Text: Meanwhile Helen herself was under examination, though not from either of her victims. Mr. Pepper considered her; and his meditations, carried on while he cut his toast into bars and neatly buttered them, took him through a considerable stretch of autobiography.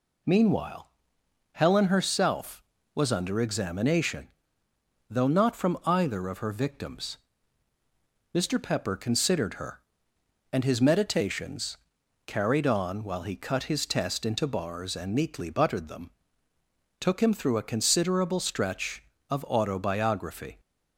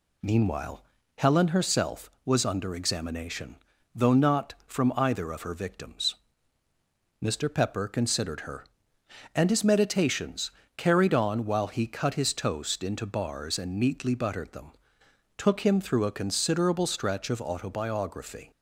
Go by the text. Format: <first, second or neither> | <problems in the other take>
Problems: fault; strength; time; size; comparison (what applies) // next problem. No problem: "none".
second | pauses between "Meanwhile" and "Helen"; noticeable; at 0.8 s; 0.62 s long; slight in the second // says "test" for "toast"; at 13.8 s